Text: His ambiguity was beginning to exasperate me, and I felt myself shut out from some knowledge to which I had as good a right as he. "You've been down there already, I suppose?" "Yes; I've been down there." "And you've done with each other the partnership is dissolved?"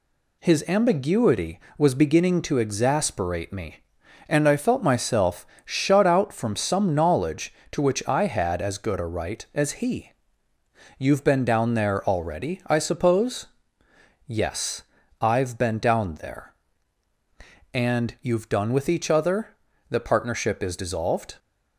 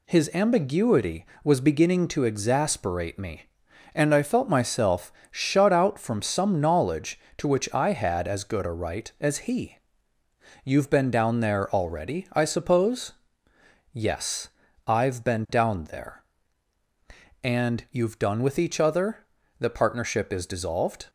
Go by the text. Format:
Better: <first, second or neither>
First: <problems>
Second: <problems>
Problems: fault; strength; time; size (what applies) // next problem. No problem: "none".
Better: neither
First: pauses between "myself" and "shut"; slight; at 5.4 s; 0.20 s long // pauses between "other" and "the"; at 19.4 s; 0.42 s long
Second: pauses between "myself" and "shut"; slight; at 5.1 s; 0.20 s long // pauses between "other" and "the"; at 19.1 s; 0.42 s long